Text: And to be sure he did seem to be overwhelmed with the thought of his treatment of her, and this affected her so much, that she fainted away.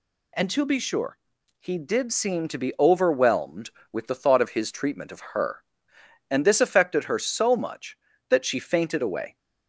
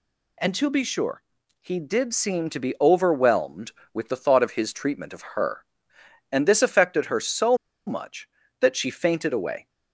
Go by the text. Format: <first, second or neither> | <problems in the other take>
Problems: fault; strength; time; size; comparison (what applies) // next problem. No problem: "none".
first | pauses between "sure" and "he"; at 1.2 s; 0.40 s long; also in the first // pauses between "so" and "much"; slight; at 7.5 s; 0.29 s long